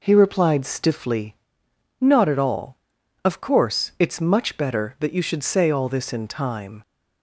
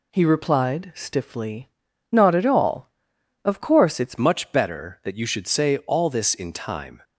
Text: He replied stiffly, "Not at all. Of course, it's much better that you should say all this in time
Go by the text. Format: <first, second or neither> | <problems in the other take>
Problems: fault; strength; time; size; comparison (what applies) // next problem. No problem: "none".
first | changes voice at "much"; from 4.1 s on; 2.9 s long